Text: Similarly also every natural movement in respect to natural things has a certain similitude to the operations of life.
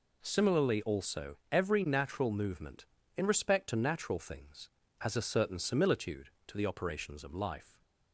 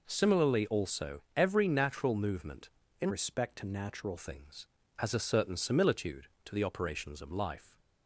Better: first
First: none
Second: changes voice from "respect" to "natural"; from 3.0 to 4.1 s; 1.1 s long

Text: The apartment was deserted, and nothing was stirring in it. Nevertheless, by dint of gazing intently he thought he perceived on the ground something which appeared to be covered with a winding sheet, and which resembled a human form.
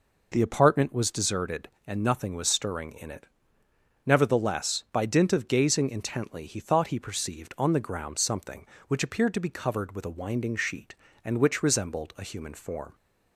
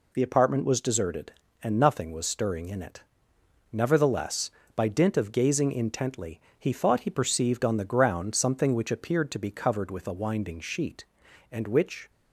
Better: first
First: none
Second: pauses between "intently" and "he"; slight; at 6.3 s; 0.20 s long // stops before "resembled a human form"; at 12.0 s

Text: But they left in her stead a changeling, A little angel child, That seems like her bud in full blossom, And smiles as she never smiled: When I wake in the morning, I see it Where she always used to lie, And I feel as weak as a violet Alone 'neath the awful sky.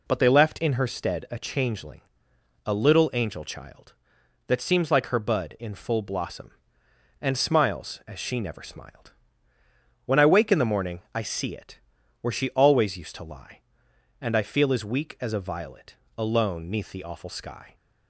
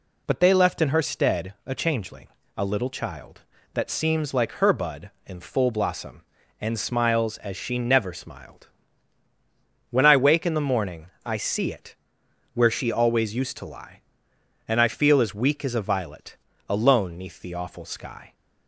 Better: first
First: pauses between "it" and "Where"; at 11.7 s; 0.42 s long // pauses between "violet" and "Alone"; slight; at 15.9 s; 0.22 s long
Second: skips "angel"; at 2.8 s // pauses between "it" and "Where"; noticeable; at 11.9 s; 0.60 s long // pauses between "violet" and "Alone"; slight; at 16.3 s; 0.30 s long

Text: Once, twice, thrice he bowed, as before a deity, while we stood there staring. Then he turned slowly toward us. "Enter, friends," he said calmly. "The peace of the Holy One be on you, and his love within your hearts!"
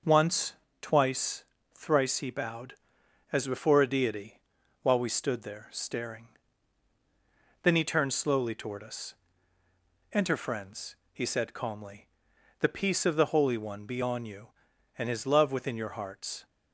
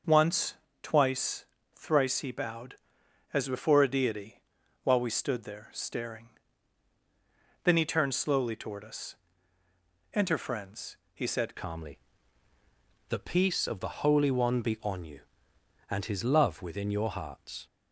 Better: first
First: none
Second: starts louder than the rest; noticeable; until 1.3 s; 6 dB // changes voice at "calmly"; from 11.5 s on; 6.1 s long

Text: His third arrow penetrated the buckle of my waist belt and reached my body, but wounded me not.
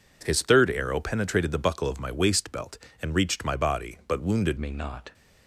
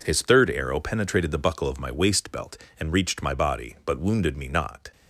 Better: second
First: changes voice at "me"; from 4.5 s on; 0.6 s long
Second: none

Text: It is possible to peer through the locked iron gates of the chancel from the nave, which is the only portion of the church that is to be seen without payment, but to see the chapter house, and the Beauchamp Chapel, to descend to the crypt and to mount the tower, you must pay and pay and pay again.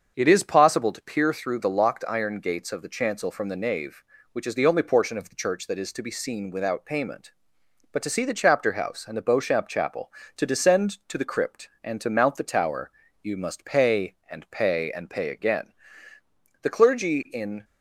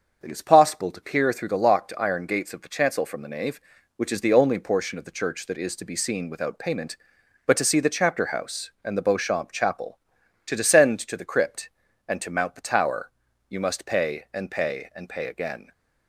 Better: second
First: starts louder than the rest; until 1.1 s; 7 dB // goes on to say "The clergy in"; noticeable; from 16.6 s on; 1.0 s long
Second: starts louder than the rest; until 1.2 s; 6.5 dB

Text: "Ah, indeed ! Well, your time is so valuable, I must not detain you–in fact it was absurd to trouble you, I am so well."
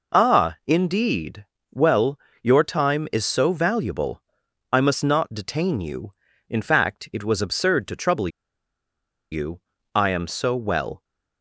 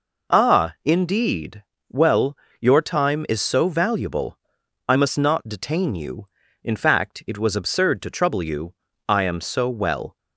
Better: second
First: pauses between "trouble" and "you"; at 8.2 s; 1.0 s long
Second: none

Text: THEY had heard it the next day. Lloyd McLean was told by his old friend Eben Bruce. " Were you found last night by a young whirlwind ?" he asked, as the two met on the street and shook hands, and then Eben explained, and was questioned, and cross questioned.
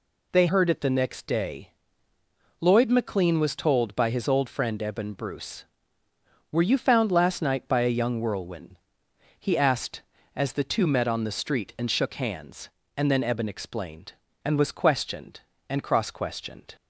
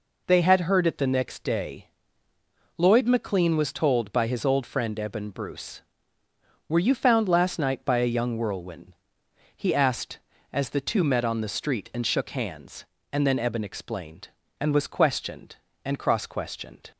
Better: second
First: skips "had"; at 0.4 s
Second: none

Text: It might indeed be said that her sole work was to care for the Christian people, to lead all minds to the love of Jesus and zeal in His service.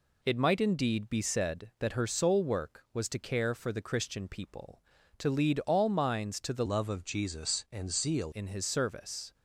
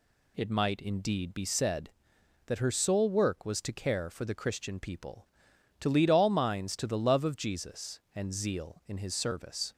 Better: second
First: changes voice from "love" to "zeal"; from 6.6 to 8.3 s; 1.7 s long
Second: none

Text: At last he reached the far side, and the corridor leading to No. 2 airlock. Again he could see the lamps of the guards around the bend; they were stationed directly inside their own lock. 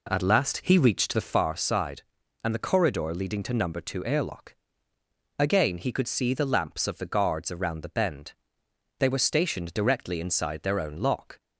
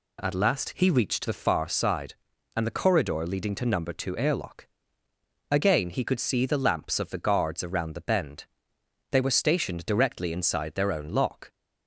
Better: second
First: starts louder than the rest; slight; until 1.4 s; 3.5 dB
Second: none

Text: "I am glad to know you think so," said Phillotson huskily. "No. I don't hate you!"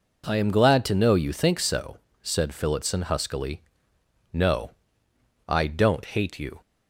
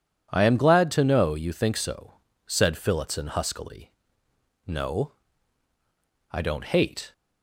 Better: first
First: none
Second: stops before "you"; at 7.1 s

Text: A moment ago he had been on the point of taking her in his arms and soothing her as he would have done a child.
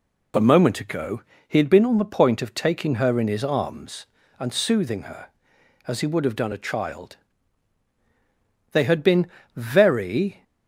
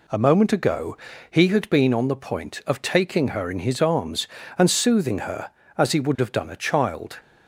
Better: second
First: pauses between "ago" and "he"; slight; at 1.2 s; 0.26 s long // goes on to say "They had been very"; strong; from 8.7 s on; 1.7 s long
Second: pauses between "ago" and "he"; slight; at 0.9 s; 0.34 s long

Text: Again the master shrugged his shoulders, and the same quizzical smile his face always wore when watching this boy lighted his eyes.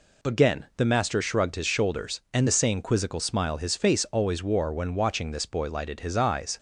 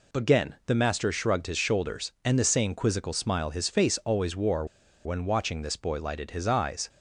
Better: first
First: none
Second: pauses between "wore" and "when"; at 4.6 s; 0.38 s long

